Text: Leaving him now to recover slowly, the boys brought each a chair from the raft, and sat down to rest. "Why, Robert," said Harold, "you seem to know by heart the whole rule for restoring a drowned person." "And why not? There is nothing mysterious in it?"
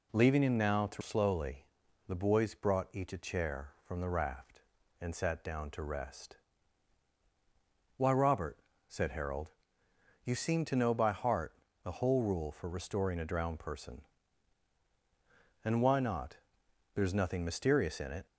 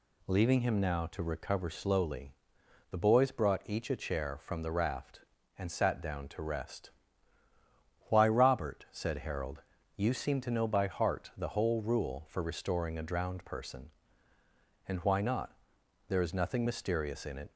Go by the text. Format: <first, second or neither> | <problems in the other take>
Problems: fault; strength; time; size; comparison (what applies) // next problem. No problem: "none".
second | skips "recover"; at 1.0 s // pauses between "heart" and "the"; slight; at 11.5 s; 0.30 s long